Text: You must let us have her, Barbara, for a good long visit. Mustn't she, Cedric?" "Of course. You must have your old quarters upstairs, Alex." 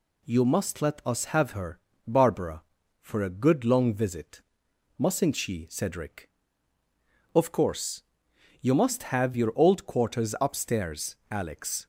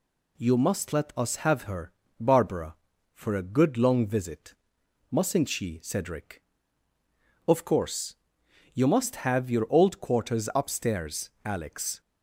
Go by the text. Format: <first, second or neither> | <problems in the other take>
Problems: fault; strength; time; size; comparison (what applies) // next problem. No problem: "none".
neither | none